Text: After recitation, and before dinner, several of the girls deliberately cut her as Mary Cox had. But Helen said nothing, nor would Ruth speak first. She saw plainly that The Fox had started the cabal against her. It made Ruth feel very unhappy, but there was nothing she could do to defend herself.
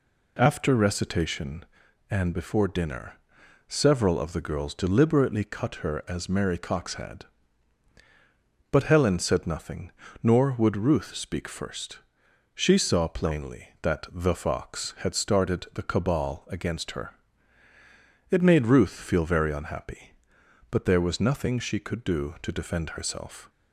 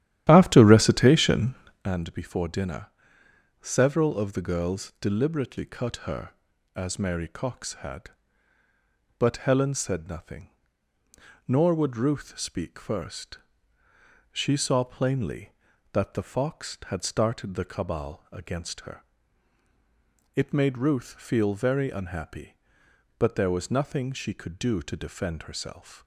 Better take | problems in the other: first | starts louder than the rest; strong; until 1.9 s; 12 dB

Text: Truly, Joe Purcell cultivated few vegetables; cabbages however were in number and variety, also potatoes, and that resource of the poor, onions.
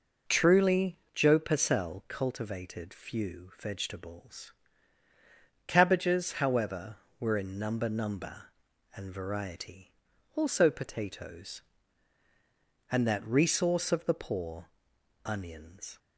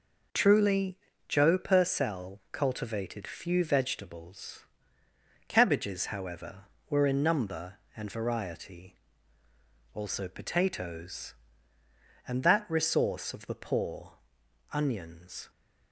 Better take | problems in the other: second | says "number" twice; at 7.8 s

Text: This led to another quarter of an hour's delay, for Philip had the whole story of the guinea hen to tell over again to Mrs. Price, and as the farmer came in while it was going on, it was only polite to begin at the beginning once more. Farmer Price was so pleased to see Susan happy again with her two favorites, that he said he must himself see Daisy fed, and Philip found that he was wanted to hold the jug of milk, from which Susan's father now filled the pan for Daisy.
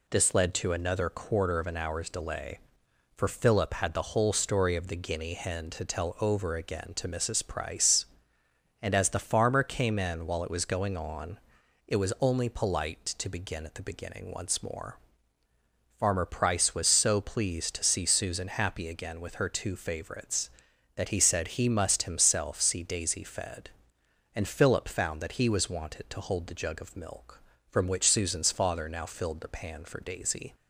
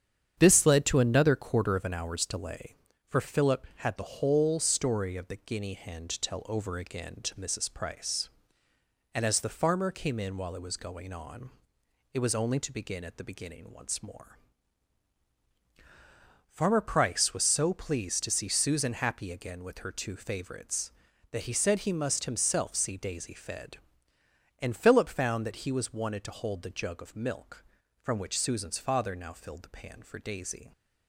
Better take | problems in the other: first | starts louder than the rest; strong; until 1.3 s; 8.5 dB // skips "polite"; at 12.6 s

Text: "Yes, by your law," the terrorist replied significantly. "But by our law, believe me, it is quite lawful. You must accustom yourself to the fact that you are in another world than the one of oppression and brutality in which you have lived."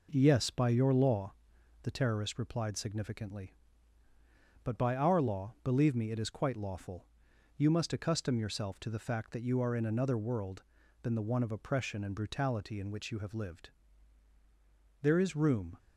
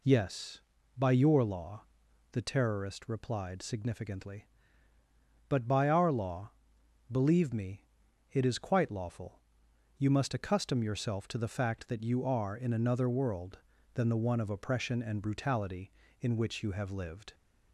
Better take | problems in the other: second | goes on to say "There is room"; noticeable; from 15.0 s on; 0.76 s long

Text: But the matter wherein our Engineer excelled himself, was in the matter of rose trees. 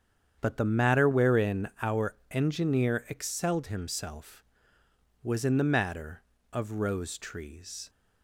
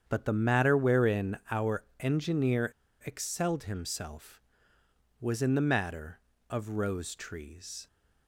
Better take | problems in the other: first | starts louder than the rest; strong; until 1.0 s; 8 dB; strong in the first // pauses between "our" and "Engineer"; slight; at 1.8 s; 0.16 s long; slight in the first // pauses between "Engineer" and "excelled"; slight; at 2.7 s; 0.32 s long

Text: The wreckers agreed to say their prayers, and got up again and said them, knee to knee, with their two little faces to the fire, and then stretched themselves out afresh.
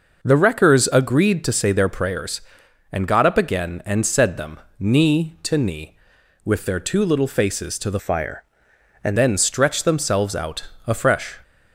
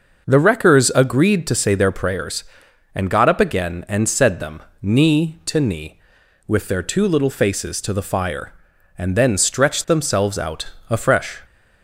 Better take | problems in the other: second | changes voice from "fire" to "and"; from 7.9 to 9.1 s; 1.2 s long // pauses between "out" and "afresh"; slight; at 10.6 s; 0.20 s long; slight in the second

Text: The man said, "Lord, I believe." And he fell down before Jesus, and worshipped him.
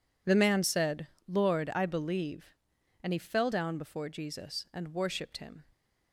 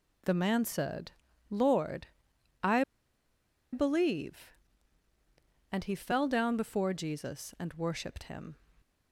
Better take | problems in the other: first | pauses between "I" and "believe"; noticeable; at 2.8 s; 0.89 s long

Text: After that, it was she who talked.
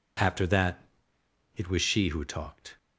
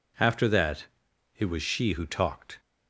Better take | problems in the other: neither | none

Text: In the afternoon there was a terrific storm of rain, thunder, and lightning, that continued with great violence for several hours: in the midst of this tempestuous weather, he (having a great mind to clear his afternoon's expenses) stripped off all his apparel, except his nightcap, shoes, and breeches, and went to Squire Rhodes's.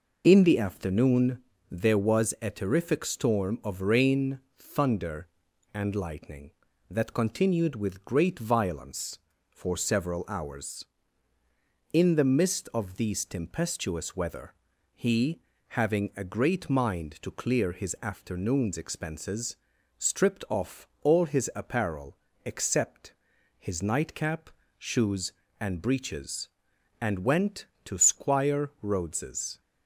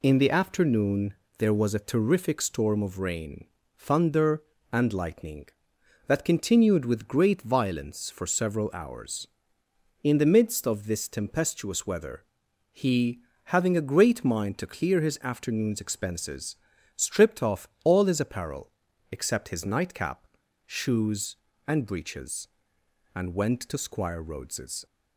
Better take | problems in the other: second | pauses between "afternoon" and "there"; slight; at 1.4 s; 0.26 s long; slight in the second // says "these" for "this"; at 12.9 s // pauses between "off" and "all"; slight; at 20.8 s; 0.16 s long; slight in the second // pauses between "except" and "his"; noticeable; at 23.1 s; 0.46 s long

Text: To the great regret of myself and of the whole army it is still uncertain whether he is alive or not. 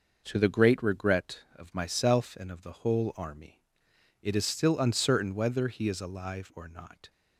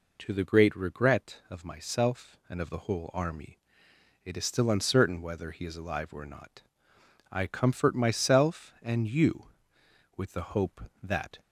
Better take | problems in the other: first | pauses between "army" and "it"; noticeable; at 3.5 s; 0.66 s long; noticeable in the first // goes on to say "I comfort myself and you with the hope that"; strong; from 7.2 s on; 4.1 s long

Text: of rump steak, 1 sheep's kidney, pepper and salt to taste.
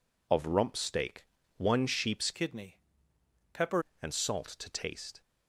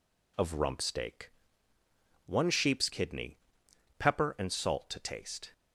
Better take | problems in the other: second | changes voice from "kidney" to "pepper"; from 2.3 to 3.8 s; 1.5 s long

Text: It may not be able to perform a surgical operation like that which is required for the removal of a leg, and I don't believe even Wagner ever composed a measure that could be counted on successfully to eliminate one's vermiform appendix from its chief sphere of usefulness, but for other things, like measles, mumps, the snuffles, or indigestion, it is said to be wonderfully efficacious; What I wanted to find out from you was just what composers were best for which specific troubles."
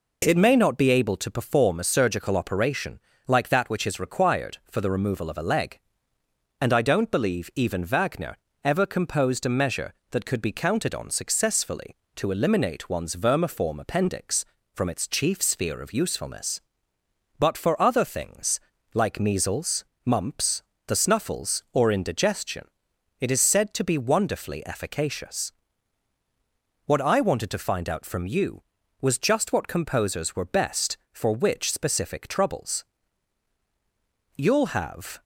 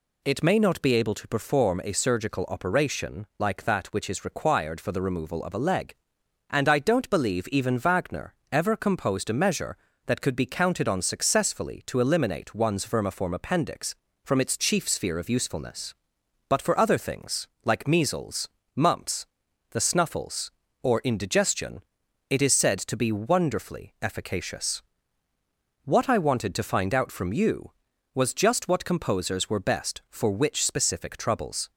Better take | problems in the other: second | pauses between "operation" and "like"; slight; at 2.9 s; 0.28 s long // pauses between "Wagner" and "ever"; slight; at 8.3 s; 0.26 s long; slight in the second // goes on to say "You'll have"; noticeable; from 34.3 s on; 0.86 s long

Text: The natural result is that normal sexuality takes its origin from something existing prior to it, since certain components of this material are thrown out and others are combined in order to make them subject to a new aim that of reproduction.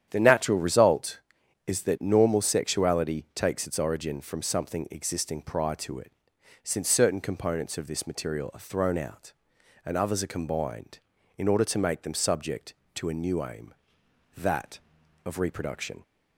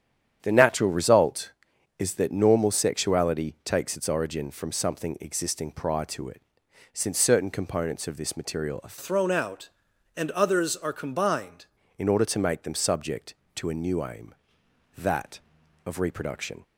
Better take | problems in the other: first | starts louder than the rest; strong; until 1.4 s; 9 dB; strong in the first // changes voice from "thrown" to "combined"; from 8.9 to 11.6 s; 2.7 s long

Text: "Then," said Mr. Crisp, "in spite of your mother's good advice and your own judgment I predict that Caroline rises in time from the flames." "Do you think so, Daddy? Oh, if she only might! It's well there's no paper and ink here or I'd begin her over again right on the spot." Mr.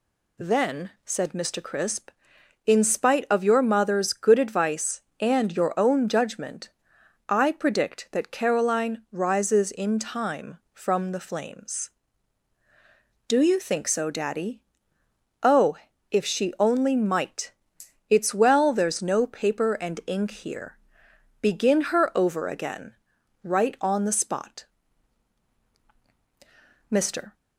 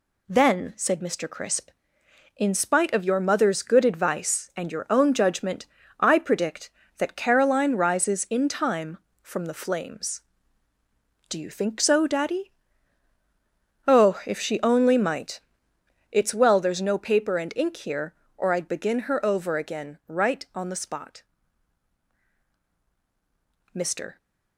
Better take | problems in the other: second | pauses between "judgment" and "I"; noticeable; at 6.6 s; 0.58 s long; slight in the second // skips "or I'd"; at 21.0 s // pauses between "again" and "right"; noticeable; at 22.9 s; 0.48 s long

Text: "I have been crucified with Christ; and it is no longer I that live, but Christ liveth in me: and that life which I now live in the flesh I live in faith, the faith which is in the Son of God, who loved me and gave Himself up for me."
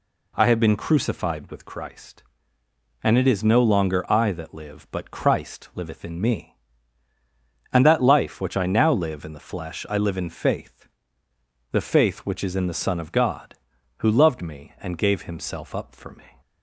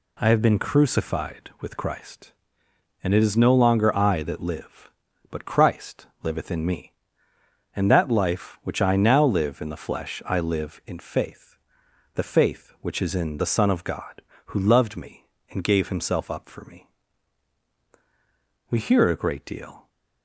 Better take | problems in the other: first | pauses between "Christ" and "liveth"; slight; at 6.0 s; 0.16 s long // goes on to say "We hear a great deal"; noticeable; from 18.7 s on; 1.1 s long

